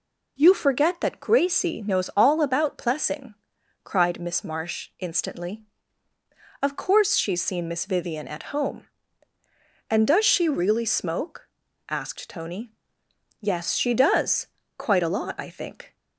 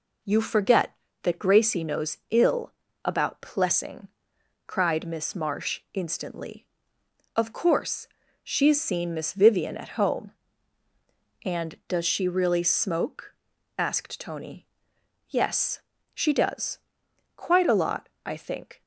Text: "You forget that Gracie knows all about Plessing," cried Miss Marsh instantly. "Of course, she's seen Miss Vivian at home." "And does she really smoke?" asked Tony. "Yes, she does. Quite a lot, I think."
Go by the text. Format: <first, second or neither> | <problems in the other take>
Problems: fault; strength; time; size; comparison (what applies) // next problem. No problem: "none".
first | says "ill" for "all"; at 2.2 s